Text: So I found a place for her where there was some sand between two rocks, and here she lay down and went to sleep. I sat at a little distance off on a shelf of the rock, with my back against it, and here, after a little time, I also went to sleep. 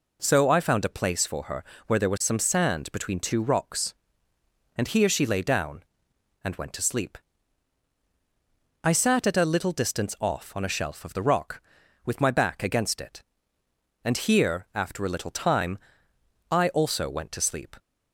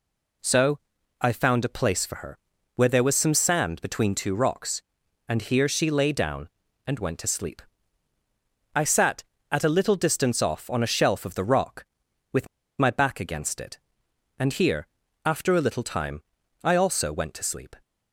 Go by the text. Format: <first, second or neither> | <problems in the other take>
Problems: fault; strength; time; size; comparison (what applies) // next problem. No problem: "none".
first | pauses between "So" and "I"; at 0.7 s; 0.42 s long // pauses between "her" and "where"; slight; at 2.3 s; 0.36 s long; slight in the first // pauses between "with" and "my"; slight; at 12.4 s; 0.32 s long